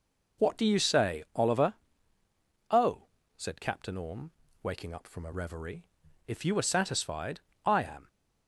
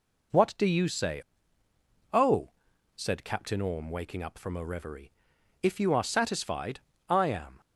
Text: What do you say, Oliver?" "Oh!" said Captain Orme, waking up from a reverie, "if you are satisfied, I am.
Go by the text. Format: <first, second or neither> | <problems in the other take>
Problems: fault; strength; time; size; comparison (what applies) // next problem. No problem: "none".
first | skips "Oliver"; at 1.6 s